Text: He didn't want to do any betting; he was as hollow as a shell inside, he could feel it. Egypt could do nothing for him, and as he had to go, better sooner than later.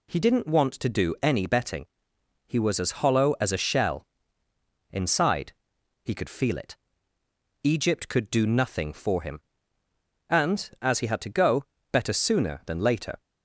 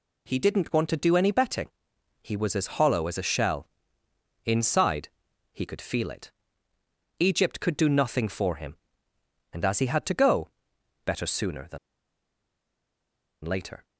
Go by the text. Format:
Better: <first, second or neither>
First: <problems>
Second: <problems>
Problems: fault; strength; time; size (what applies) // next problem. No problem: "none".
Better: first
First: pauses between "shell" and "inside"; noticeable; at 4.0 s; 0.84 s long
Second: pauses between "shell" and "inside"; noticeable; at 3.6 s; 0.74 s long // pauses between "than" and "later"; strong; at 11.7 s; 1.6 s long